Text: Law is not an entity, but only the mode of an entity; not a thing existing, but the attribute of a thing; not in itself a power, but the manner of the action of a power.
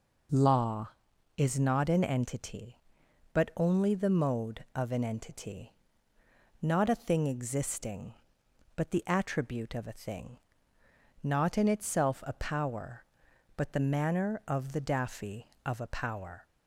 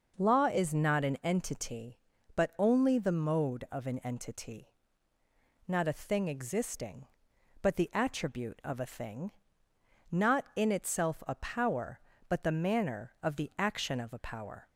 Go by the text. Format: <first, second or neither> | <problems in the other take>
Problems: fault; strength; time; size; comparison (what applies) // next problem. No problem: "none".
second | says "daffy" for "action"; at 14.8 s